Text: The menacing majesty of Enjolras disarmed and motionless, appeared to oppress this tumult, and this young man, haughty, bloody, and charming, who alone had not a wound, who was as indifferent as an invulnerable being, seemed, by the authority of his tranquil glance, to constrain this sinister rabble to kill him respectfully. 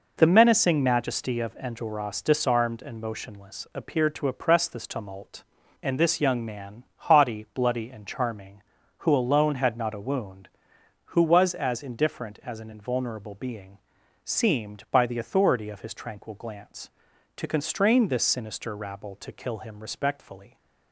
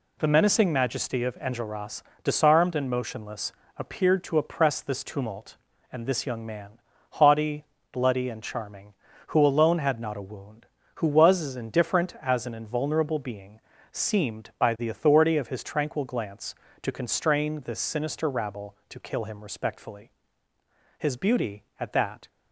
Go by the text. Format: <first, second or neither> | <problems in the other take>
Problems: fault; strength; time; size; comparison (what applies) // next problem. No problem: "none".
first | pauses between "Enjolras" and "disarmed"; slight; at 2.0 s; 0.22 s long // goes on to say "His beauty at that"; noticeable; from 20.9 s on; 1.3 s long